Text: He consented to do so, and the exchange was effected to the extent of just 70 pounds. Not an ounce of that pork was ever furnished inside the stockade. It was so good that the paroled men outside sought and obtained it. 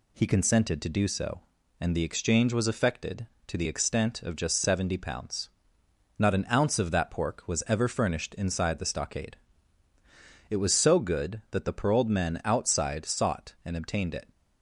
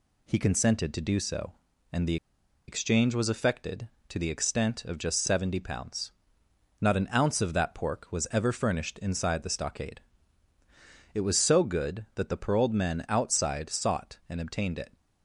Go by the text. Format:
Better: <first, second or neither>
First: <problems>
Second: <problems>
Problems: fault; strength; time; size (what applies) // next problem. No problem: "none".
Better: first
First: none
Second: pauses between "the" and "exchange"; noticeable; at 2.1 s; 0.52 s long